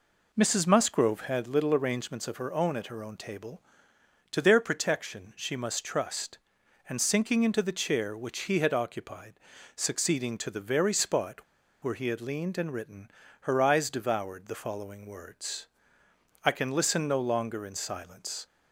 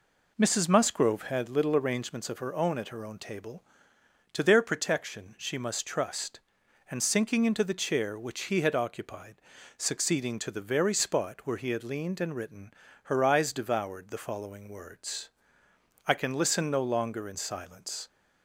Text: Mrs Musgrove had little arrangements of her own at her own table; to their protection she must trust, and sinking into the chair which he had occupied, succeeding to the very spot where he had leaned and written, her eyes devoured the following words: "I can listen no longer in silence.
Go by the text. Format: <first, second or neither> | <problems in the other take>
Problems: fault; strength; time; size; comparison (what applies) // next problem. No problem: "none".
second | pauses between "spot" and "where"; at 11.4 s; 0.38 s long